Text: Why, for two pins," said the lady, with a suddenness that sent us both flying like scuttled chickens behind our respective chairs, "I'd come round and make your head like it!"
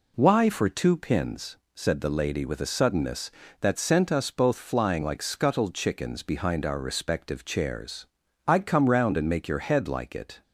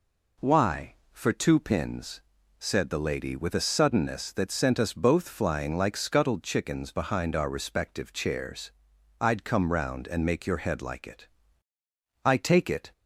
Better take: first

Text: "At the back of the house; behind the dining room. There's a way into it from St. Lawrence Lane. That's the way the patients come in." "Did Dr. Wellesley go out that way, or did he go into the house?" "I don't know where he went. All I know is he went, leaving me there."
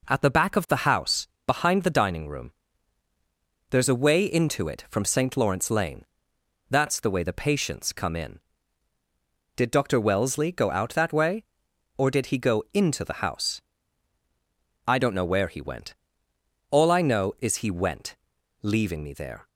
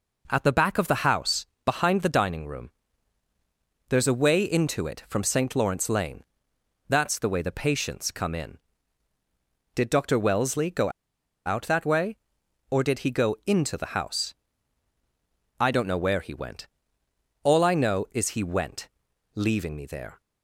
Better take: first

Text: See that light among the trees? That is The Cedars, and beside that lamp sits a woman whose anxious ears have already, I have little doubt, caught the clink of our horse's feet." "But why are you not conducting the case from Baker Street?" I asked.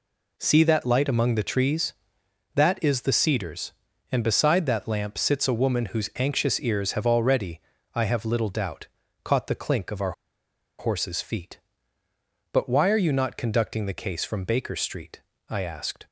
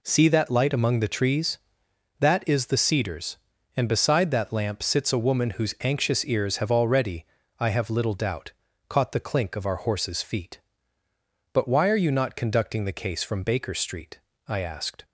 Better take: second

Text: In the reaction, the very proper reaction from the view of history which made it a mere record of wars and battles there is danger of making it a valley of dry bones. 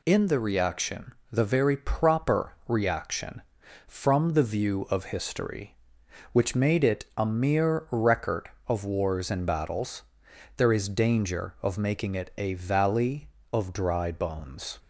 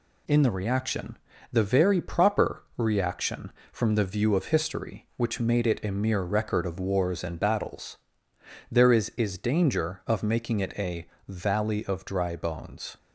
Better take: first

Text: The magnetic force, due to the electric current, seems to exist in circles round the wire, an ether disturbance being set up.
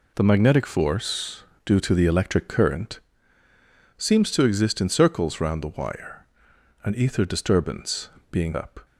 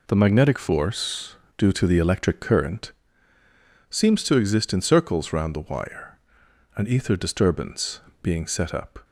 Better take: second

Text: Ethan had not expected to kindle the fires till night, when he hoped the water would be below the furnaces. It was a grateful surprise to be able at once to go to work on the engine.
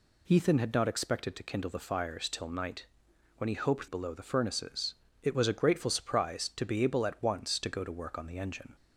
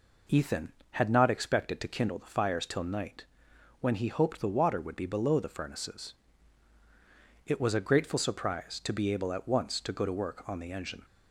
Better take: second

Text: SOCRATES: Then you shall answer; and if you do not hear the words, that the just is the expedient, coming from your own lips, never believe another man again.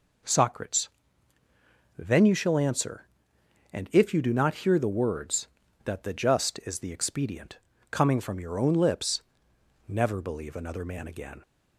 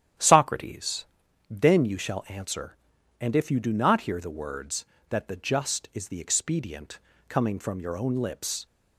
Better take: first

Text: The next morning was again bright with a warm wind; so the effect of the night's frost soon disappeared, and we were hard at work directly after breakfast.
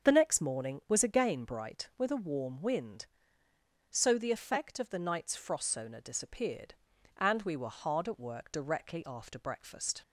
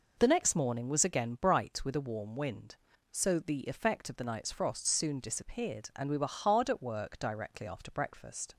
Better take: second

